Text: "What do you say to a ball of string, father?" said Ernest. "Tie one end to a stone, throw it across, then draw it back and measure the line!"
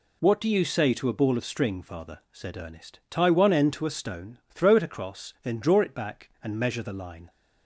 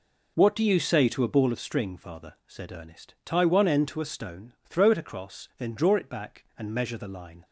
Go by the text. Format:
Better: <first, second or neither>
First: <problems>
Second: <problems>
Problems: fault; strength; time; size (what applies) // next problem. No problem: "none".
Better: first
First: none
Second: starts louder than the rest; noticeable; until 1.6 s; 5 dB